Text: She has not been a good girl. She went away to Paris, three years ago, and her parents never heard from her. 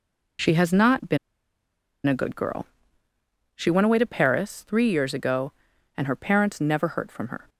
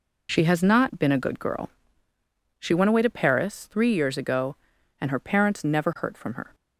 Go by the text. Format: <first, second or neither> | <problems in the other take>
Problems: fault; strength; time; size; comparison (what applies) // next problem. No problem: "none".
second | pauses between "been" and "a"; noticeable; at 1.1 s; 0.88 s long